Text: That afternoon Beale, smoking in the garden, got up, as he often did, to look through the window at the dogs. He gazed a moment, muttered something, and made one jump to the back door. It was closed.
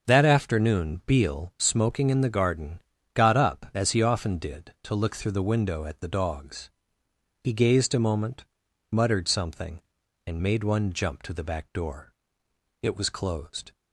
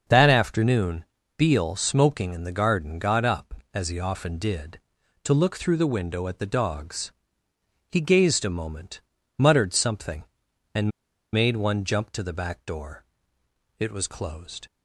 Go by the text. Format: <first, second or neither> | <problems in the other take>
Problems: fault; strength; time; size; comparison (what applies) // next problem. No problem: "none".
first | starts louder than the rest; until 1.4 s; 6.5 dB; also in the first // pauses between "afternoon" and "Beale"; slight; at 1.0 s; 0.32 s long // pauses between "and" and "made"; at 10.8 s; 0.43 s long